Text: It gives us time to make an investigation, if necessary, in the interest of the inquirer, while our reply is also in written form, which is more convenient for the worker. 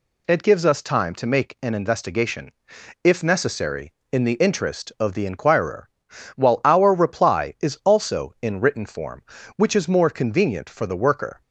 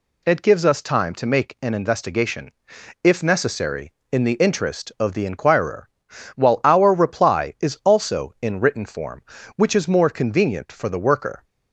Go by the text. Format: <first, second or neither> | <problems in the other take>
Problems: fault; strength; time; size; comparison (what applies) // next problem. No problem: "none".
neither | none